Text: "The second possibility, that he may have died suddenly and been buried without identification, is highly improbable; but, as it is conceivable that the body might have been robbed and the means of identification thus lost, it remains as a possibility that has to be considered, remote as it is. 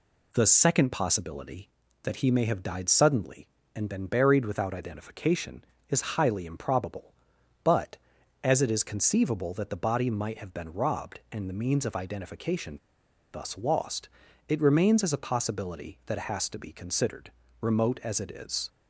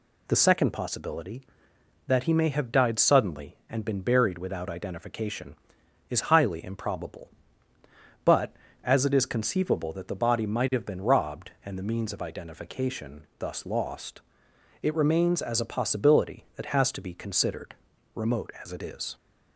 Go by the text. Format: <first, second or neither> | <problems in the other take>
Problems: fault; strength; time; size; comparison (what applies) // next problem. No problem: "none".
second | pauses between "identification" and "thus"; noticeable; at 12.7 s; 0.55 s long